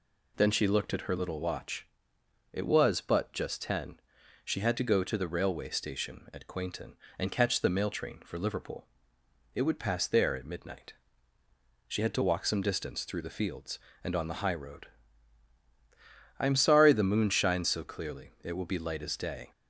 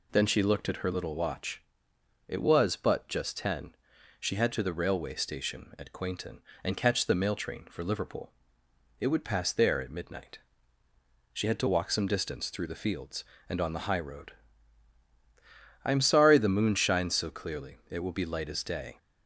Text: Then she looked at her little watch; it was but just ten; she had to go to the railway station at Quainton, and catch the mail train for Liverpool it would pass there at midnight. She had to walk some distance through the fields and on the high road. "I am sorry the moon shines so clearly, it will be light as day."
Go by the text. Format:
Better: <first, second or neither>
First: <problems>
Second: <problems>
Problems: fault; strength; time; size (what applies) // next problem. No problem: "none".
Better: first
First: pauses between "Liverpool" and "it"; noticeable; at 8.8 s; 0.68 s long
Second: skips "to go"; at 4.5 s // pauses between "Liverpool" and "it"; noticeable; at 8.3 s; 0.68 s long